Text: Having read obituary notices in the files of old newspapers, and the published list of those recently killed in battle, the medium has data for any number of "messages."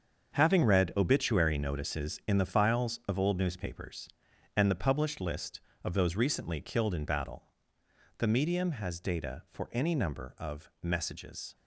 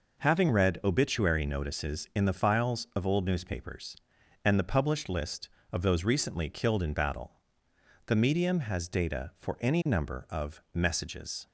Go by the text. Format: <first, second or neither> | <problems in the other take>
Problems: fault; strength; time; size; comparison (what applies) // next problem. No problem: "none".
second | gets quieter; strong; throughout; 10 dB